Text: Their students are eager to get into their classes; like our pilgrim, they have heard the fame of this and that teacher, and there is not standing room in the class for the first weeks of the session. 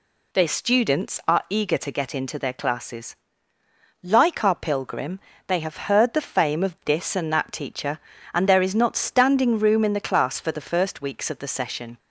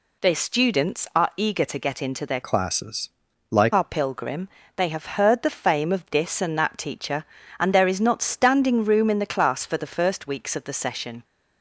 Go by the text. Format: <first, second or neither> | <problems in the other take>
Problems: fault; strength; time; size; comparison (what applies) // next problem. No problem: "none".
first | changes voice from "classes" to "like"; from 2.4 to 3.7 s; 1.3 s long